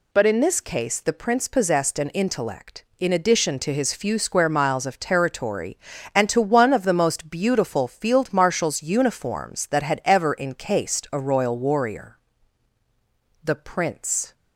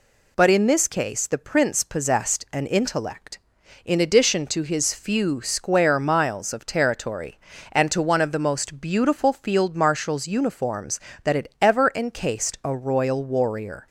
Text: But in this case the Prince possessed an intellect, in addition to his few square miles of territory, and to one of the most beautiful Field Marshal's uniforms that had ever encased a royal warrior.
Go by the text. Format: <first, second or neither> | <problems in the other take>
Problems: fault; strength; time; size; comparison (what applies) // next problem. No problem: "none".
second | goes on to say "The Prince"; noticeable; from 13.4 s on; 0.90 s long